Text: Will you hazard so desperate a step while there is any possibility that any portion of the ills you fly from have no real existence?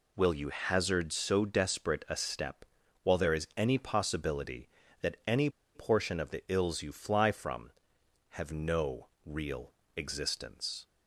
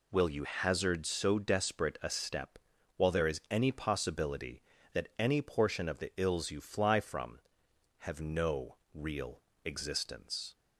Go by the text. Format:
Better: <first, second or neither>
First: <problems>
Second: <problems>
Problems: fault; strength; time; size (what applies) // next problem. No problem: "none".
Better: second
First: pauses between "step" and "while"; at 2.6 s; 0.38 s long // pauses between "any" and "portion"; slight; at 5.4 s; 0.25 s long // pauses between "no" and "real"; slight; at 9.0 s; 0.18 s long // pauses between "real" and "existence"; slight; at 9.7 s; 0.24 s long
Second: pauses between "step" and "while"; at 2.5 s; 0.38 s long // pauses between "no" and "real"; slight; at 8.7 s; 0.18 s long // pauses between "real" and "existence"; slight; at 9.4 s; 0.24 s long